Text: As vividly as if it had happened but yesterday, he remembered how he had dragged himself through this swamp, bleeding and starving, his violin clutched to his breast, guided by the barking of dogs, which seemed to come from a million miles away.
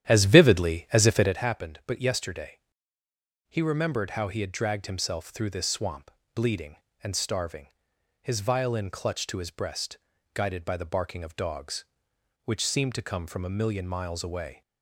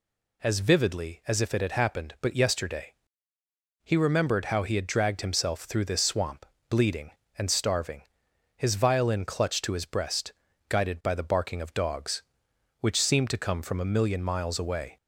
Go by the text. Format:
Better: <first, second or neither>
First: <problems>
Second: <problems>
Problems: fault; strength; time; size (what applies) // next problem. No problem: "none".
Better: second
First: starts louder than the rest; strong; until 1.4 s; 10.5 dB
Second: none